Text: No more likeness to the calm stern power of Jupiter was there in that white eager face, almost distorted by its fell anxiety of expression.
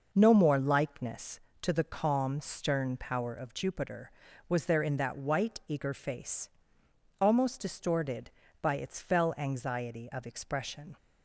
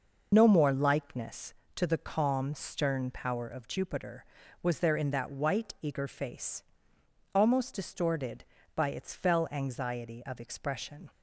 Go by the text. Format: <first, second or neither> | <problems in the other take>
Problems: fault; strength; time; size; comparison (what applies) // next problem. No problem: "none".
first | loses the start of "No"; at 0.3 s; 45 ms